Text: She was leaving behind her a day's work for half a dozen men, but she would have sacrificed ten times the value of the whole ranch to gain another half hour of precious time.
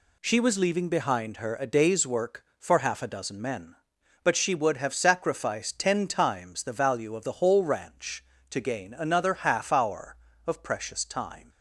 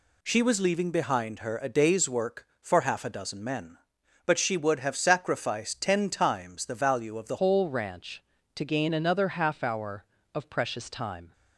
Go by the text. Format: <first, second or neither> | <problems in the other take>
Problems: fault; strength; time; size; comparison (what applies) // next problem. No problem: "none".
first | changes voice at "whole"; from 7.3 s on; 4.0 s long